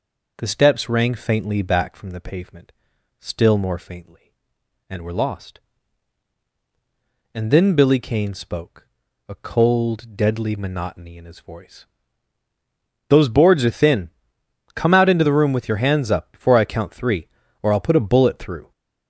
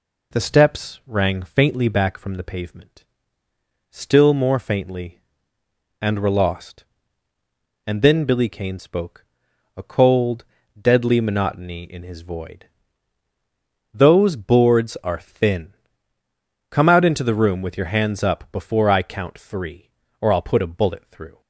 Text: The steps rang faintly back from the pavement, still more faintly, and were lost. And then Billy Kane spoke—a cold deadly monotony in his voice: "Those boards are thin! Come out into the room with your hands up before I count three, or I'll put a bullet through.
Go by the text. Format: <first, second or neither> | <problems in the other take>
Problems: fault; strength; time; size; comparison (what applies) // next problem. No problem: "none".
first | pauses between "cold" and "deadly"; slight; at 10.4 s; 0.36 s long // says "void" for "voice"; at 12.2 s